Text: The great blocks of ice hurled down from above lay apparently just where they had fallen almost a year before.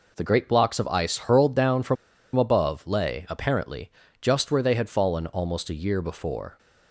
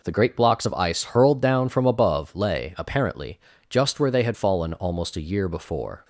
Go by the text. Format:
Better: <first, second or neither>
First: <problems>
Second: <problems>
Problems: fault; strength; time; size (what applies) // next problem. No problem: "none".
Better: second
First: pauses between "from" and "above"; at 1.9 s; 0.40 s long // pauses between "apparently" and "just"; slight; at 3.8 s; 0.30 s long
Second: pauses between "apparently" and "just"; slight; at 3.3 s; 0.30 s long